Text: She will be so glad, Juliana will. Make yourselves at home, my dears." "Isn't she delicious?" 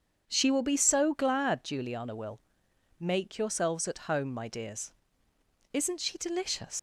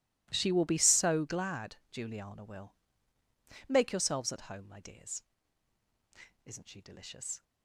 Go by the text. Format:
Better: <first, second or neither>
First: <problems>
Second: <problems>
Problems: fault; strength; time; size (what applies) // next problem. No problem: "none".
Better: second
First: starts louder than the rest; strong; until 1.2 s; 7 dB // leaves "delicious" unfinished; at 6.7 s; 115 ms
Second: none